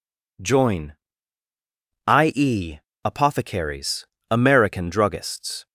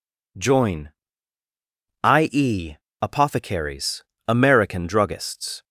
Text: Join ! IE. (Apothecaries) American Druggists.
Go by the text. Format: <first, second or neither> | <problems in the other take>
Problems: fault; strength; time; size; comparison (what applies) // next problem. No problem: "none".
neither | none